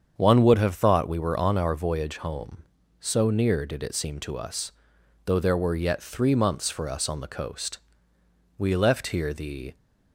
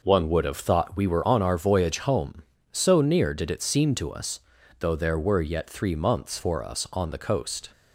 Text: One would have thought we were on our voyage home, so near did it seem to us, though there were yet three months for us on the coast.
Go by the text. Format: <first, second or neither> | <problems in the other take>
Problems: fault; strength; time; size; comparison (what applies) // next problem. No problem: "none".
second | starts louder than the rest; strong; until 1.2 s; 7.5 dB // goes on to say "We left here the"; noticeable; from 8.5 s on; 1.1 s long